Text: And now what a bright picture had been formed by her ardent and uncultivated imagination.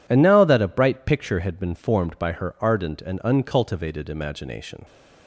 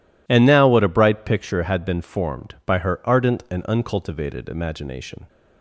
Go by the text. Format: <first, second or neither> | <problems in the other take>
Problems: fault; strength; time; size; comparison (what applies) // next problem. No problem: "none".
second | says "that" for "what"; at 0.4 s